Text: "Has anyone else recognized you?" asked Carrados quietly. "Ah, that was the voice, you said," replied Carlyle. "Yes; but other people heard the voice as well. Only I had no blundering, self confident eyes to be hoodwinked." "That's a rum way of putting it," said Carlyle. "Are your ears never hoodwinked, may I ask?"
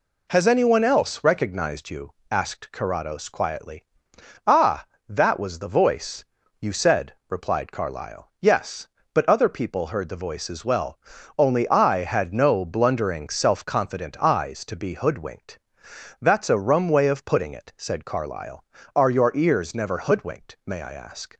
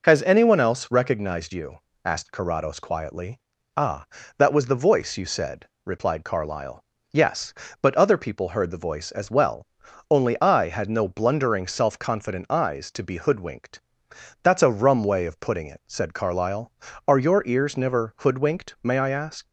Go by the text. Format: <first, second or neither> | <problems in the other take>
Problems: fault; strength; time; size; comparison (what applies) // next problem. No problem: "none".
neither | none